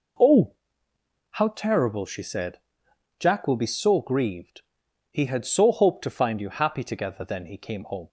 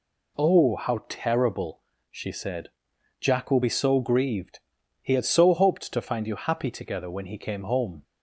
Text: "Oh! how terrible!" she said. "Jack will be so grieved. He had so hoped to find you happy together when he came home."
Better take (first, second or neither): second